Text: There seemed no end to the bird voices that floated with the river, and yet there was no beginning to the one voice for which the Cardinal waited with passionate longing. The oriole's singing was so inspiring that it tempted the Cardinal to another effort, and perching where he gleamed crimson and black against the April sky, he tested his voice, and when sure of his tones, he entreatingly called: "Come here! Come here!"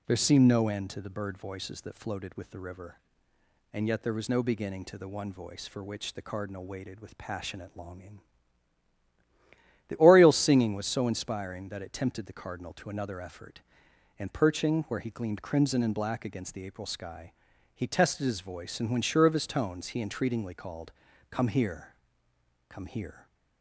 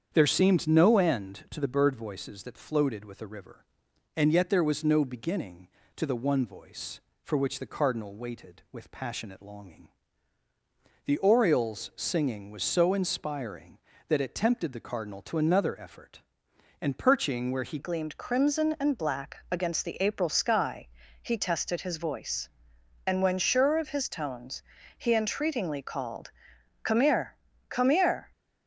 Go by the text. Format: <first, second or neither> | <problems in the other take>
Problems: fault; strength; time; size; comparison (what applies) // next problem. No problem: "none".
first | starts louder than the rest; strong; until 1.1 s; 7.5 dB // changes voice at "gleamed"; from 17.7 s on; 10.6 s long